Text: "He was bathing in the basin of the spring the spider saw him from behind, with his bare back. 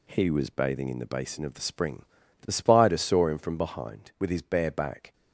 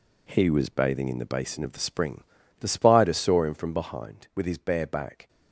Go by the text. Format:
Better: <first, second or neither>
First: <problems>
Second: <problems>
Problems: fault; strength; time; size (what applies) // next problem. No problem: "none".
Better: first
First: pauses between "spring" and "the"; slight; at 2.0 s; 0.34 s long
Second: gets quieter; strong; throughout; 8 dB // pauses between "spring" and "the"; slight; at 2.2 s; 0.34 s long